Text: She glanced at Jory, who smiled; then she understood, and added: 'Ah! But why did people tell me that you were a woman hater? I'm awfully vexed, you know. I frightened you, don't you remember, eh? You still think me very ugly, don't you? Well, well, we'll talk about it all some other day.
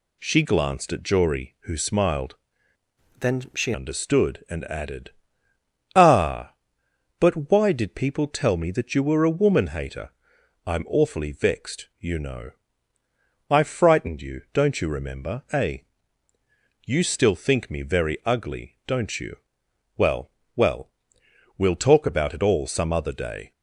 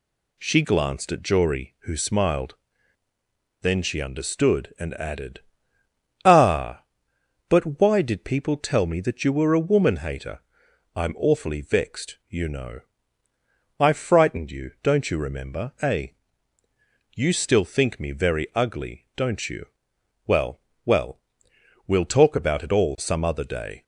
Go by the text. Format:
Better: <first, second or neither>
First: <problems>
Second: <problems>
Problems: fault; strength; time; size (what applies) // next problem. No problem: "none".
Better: second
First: changes voice from "then" to "she"; from 3.1 to 3.7 s; 0.6 s long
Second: none